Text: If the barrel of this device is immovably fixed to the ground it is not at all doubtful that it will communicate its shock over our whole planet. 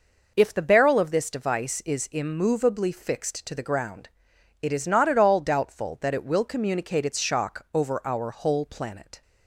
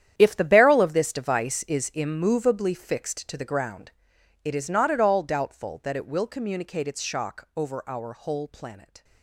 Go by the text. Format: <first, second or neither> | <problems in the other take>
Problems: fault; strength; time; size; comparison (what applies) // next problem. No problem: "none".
first | gets quieter; strong; throughout; 15.5 dB // pauses between "ground" and "it"; noticeable; at 3.9 s; 0.54 s long; noticeable in the first